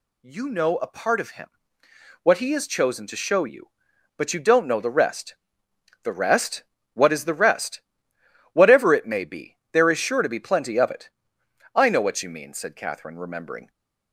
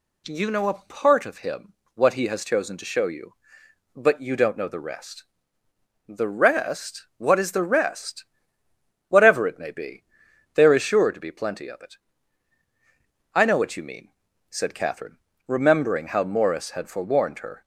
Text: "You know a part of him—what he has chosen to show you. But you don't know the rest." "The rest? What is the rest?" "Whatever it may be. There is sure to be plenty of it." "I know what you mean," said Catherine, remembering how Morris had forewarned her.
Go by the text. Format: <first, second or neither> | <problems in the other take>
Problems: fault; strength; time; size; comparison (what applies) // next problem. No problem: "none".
second | stops before "how Morris had forewarned her"; at 13.7 s